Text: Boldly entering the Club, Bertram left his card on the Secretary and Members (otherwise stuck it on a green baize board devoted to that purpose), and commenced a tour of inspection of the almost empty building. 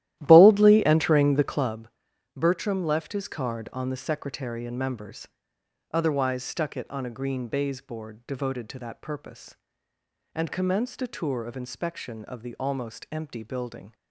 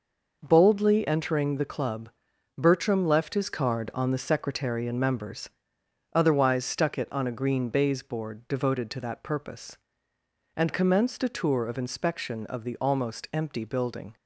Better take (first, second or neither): second